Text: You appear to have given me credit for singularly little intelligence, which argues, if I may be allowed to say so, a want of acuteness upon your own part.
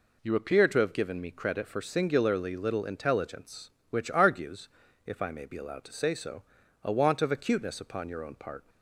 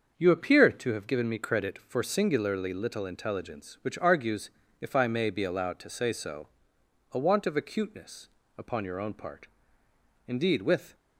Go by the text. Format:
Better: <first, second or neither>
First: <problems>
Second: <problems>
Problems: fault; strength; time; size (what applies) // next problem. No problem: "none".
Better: first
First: none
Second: starts louder than the rest; until 1.1 s; 6.5 dB // pauses between "acuteness" and "upon"; slight; at 8.2 s; 0.28 s long // goes on to say "Indeed with"; noticeable; from 10.2 s on; 0.68 s long